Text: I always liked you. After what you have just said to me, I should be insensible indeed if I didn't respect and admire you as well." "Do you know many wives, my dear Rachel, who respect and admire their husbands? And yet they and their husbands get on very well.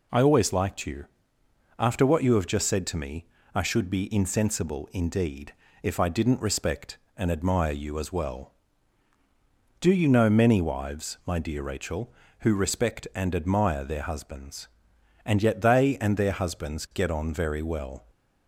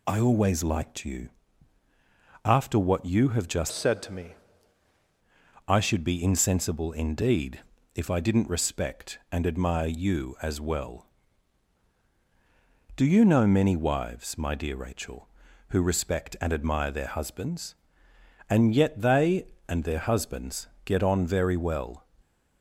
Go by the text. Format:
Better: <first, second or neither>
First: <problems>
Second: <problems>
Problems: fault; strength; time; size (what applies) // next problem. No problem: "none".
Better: first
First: pauses between "indeed" and "if"; slight; at 5.5 s; 0.30 s long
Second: changes voice from "said" to "me"; from 3.7 to 4.3 s; 0.6 s long // pauses between "indeed" and "if"; slight; at 7.6 s; 0.34 s long // pauses between "husbands" and "get"; slight; at 20.6 s; 0.18 s long